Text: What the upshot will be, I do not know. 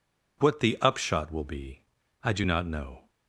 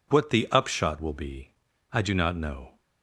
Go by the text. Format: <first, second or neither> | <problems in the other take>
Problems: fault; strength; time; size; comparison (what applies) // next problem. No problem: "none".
neither | none